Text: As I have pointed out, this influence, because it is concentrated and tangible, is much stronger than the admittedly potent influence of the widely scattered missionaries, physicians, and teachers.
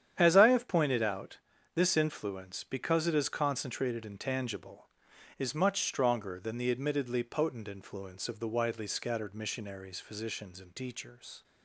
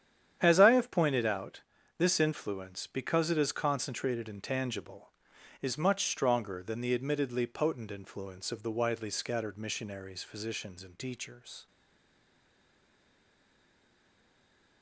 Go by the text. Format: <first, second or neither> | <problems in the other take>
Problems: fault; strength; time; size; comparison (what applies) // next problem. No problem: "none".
first | starts louder than the rest; strong; until 1.4 s; 9.5 dB; strong in the first // stays silent after the last word; strong; from 11.6 s on; 3.2 s long